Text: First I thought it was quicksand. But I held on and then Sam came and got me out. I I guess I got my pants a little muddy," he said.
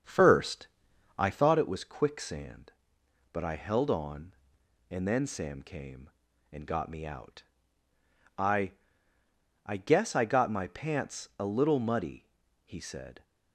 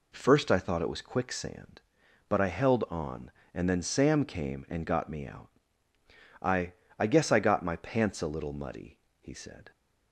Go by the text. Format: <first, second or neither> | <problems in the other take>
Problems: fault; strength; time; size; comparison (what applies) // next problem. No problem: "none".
second | starts louder than the rest; strong; until 1.6 s; 7.5 dB // pauses between "First" and "I"; noticeable; at 0.6 s; 0.50 s long // pauses between "I" and "I"; noticeable; at 8.7 s; 0.92 s long; slight in the second